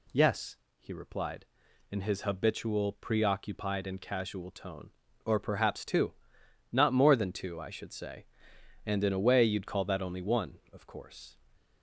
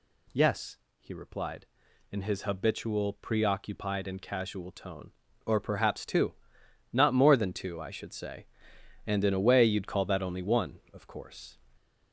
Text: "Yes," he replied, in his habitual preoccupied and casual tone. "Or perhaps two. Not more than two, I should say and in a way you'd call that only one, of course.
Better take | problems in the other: first | gets louder; throughout; 3.5 dB

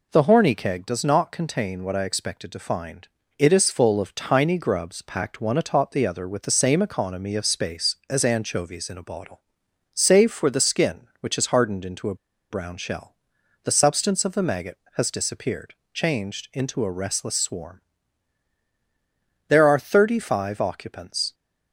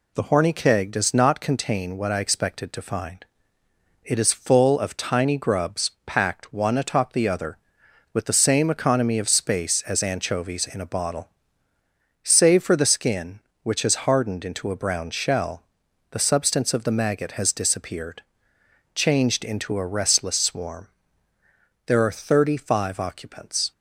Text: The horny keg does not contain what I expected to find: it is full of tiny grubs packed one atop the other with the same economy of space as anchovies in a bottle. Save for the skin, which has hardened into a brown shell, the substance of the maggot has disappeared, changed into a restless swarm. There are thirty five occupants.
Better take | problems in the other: second | pauses between "a" and "brown"; slight; at 12.1 s; 0.35 s long

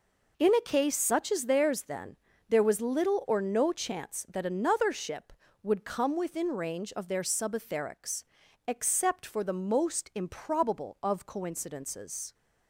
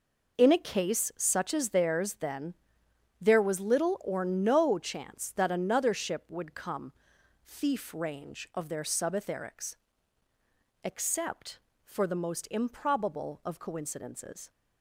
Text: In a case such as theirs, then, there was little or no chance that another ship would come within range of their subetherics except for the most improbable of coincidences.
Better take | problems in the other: first | says "thief" for "within"; at 7.4 s // pauses between "subetherics" and "except"; at 9.7 s; 1.0 s long; also in the first

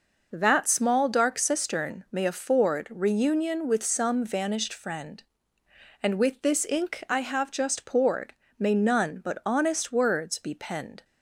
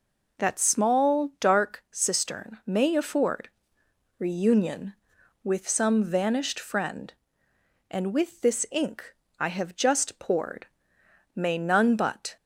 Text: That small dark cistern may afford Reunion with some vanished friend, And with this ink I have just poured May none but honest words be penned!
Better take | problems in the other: first | pauses between "afford" and "Reunion"; noticeable; at 3.5 s; 0.68 s long // pauses between "ink" and "I"; slight; at 9.1 s; 0.24 s long // pauses between "poured" and "May"; noticeable; at 10.6 s; 0.70 s long; slight in the first // stops before "honest words be penned"; at 12.3 s

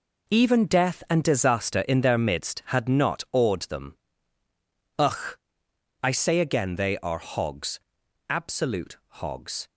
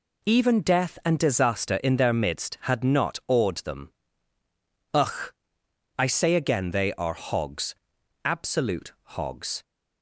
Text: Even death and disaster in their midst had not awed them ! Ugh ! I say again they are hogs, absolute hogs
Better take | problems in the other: second | gets quieter; strong; throughout; 10 dB

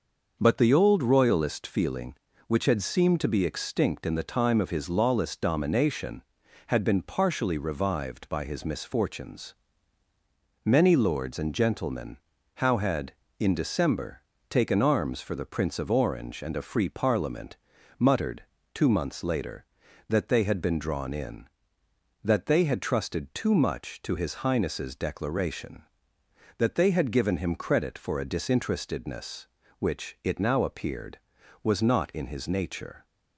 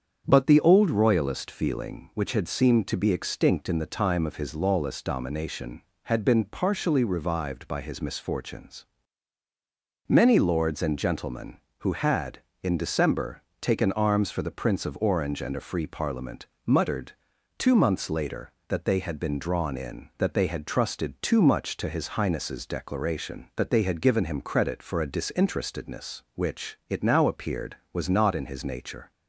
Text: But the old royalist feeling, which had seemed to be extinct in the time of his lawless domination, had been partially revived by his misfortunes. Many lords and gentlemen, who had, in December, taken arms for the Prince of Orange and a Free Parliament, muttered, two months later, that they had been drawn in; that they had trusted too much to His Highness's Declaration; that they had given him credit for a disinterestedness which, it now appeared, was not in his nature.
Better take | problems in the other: second | starts louder than the rest; noticeable; until 1.4 s; 6 dB; strong in the second // says "how" for "who"; at 12.5 s

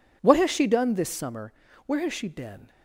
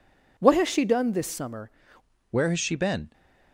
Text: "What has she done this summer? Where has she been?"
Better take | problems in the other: first | changes voice at "Where"; from 2.2 s on; 0.8 s long

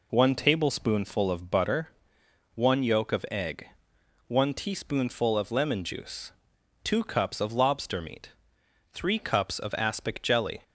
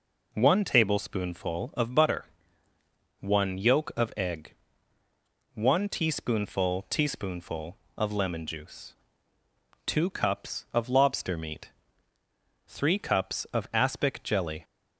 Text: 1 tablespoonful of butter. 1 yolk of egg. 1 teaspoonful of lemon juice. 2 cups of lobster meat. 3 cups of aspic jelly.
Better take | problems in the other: first | says "teaspoonful" twice; at 6.8 s

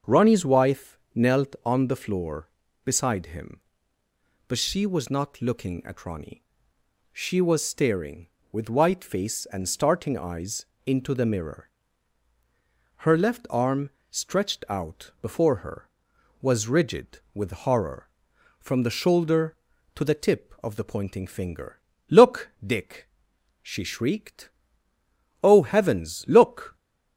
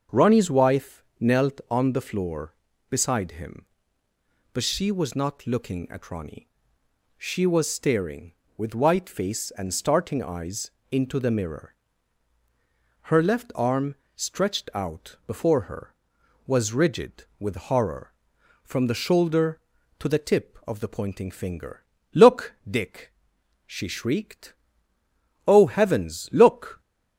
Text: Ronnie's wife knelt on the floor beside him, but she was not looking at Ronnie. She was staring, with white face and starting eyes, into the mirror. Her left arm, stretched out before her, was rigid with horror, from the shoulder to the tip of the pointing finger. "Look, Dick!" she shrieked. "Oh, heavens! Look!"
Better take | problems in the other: neither | starts louder than the rest; the same in both // pauses between "wife" and "knelt"; slight; the same in both

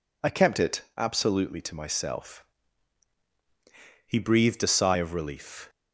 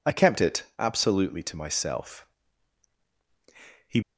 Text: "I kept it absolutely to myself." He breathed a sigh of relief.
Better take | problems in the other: first | stops before "breathed a sigh of relief"; at 4.0 s

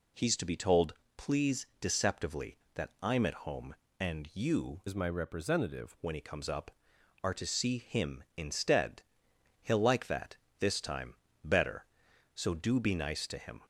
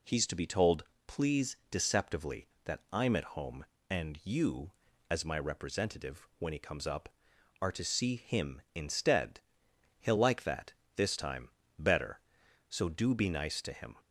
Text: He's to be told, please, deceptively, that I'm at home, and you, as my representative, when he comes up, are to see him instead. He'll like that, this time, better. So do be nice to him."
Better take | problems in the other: second | changes voice from "as" to "representative"; from 4.8 to 5.9 s; 1.1 s long

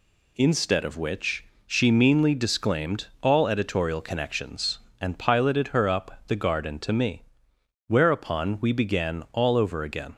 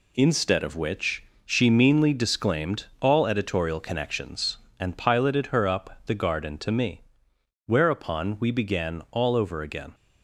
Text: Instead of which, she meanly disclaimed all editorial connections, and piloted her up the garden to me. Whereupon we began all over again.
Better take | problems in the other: first | gets quieter; throughout; 6.5 dB

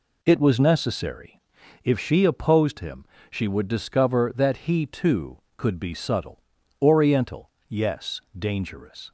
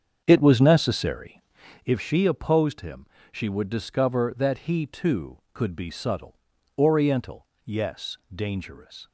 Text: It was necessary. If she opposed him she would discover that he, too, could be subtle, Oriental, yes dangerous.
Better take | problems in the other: first | starts louder than the rest; strong; until 2.0 s; 7.5 dB // pauses between "him" and "she"; slight; at 3.0 s; 0.28 s long; slight in the first // pauses between "yes" and "dangerous"; slight; at 8.1 s; 0.16 s long; slight in the first

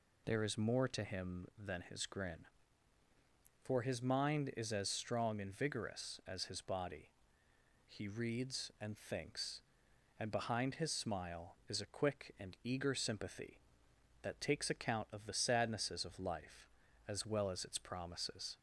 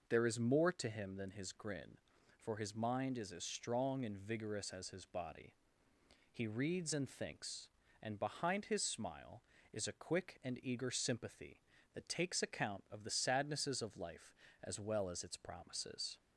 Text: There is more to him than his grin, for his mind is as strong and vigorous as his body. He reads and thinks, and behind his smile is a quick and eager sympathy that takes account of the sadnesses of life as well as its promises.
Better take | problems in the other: neither | none

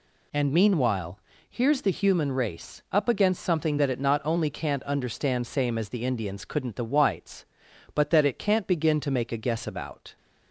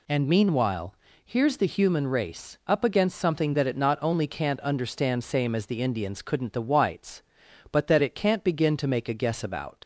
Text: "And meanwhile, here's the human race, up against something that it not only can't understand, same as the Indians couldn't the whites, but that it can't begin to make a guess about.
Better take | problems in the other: first | leaves "about" unfinished; at 9.8 s; 95 ms

